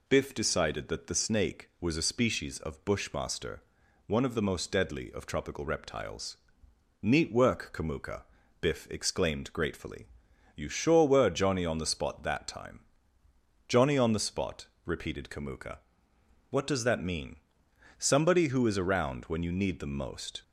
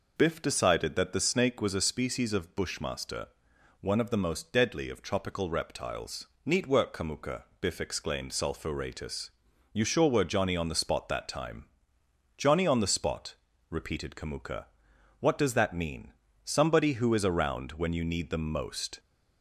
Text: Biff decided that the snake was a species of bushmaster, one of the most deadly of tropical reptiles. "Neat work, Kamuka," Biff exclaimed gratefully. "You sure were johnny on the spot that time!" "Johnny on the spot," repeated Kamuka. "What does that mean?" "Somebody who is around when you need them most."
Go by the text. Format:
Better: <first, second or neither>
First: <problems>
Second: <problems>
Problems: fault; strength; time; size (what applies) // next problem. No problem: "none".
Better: first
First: none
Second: says "sulphuratus" for "gratefully"; at 8.3 s